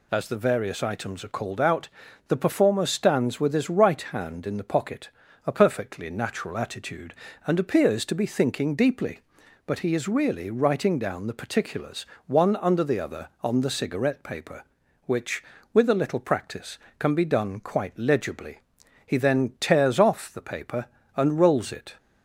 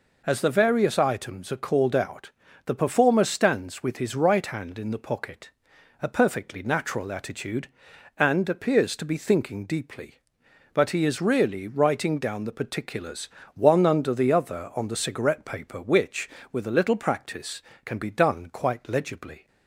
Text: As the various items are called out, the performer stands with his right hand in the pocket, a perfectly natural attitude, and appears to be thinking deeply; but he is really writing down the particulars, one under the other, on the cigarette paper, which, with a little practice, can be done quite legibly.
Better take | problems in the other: second | goes on to say "He then tears off the paper and rolls it"; strong; from 19.0 s on; 2.9 s long

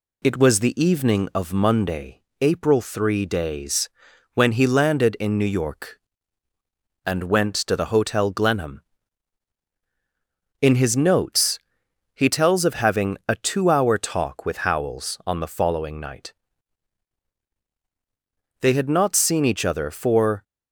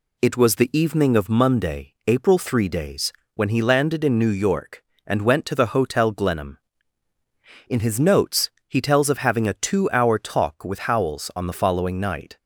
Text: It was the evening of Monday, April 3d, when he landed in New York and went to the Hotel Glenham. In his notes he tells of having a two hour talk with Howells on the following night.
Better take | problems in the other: second | pauses between "notes" and "he"; noticeable; at 11.5 s; 0.56 s long; slight in the second // goes on to say "They had not seen each other for"; strong; from 18.5 s on; 1.8 s long

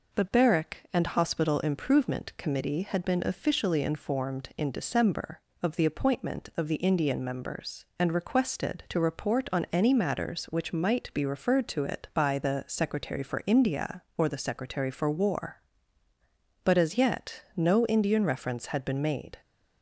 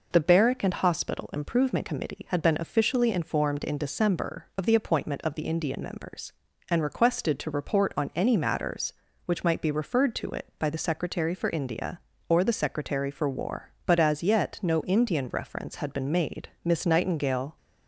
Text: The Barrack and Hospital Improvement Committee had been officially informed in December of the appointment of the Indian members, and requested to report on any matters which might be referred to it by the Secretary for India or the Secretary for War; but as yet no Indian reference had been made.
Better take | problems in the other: first | goes on to say "Miss Nightingale"; noticeable; from 16.6 s on; 0.92 s long

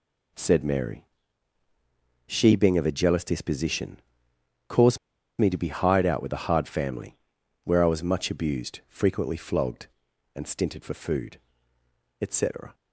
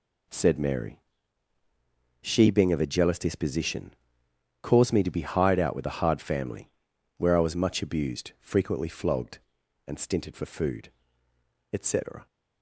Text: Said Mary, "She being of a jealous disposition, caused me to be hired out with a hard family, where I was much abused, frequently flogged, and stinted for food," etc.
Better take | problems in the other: second | pauses between "caused" and "me"; at 4.9 s; 0.41 s long

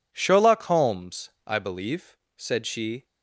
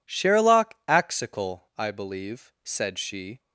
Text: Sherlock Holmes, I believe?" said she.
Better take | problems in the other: first | says "Axical" for "Holmes"; at 0.8 s

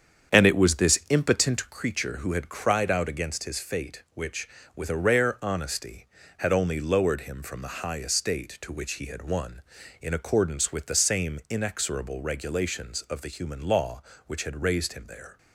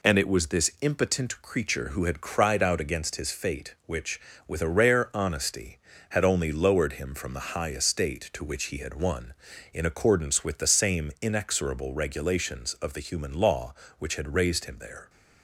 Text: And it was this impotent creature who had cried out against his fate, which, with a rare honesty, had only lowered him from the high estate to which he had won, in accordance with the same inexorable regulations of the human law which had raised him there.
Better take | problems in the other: second | starts louder than the rest; strong; until 2.0 s; 8 dB

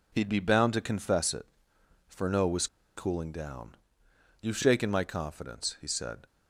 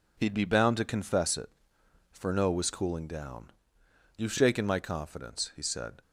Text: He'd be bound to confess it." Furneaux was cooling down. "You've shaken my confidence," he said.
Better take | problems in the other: second | pauses between "was" and "cooling"; slight; at 2.6 s; 0.29 s long

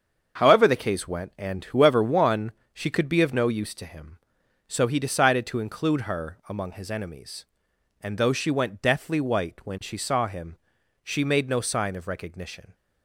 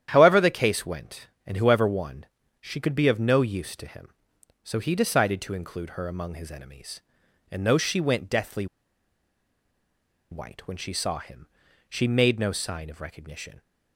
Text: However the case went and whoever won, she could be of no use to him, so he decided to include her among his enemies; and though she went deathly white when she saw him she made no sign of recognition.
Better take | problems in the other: first | starts louder than the rest; strong; until 1.1 s; 10 dB; also in the first // pauses between "deathly" and "white"; strong; at 8.6 s; 1.6 s long // pauses between "him" and "she"; at 11.4 s; 0.42 s long; noticeable in the first

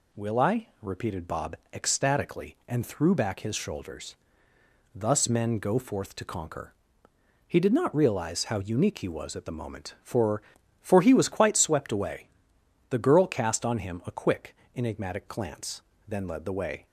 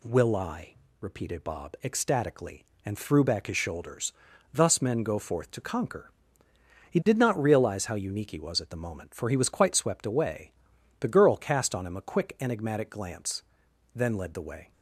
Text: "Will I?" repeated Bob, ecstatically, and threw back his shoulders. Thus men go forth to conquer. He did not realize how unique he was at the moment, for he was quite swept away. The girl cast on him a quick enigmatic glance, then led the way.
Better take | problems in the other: second | says "for" twice; at 10.8 s // pauses between "quick" and "enigmatic"; slight; at 14.5 s; 0.18 s long

